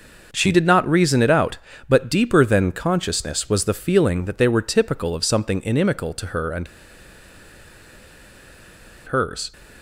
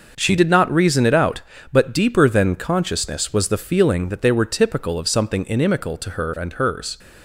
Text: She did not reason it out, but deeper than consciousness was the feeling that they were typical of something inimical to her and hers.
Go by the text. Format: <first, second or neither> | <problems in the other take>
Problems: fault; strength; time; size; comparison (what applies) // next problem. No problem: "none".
second | pauses between "and" and "hers"; strong; at 6.6 s; 2.4 s long